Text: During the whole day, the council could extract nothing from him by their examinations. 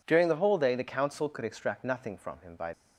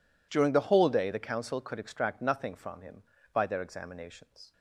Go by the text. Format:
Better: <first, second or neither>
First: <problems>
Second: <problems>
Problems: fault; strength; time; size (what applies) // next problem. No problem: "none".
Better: second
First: stops before "their examinations"; at 2.7 s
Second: none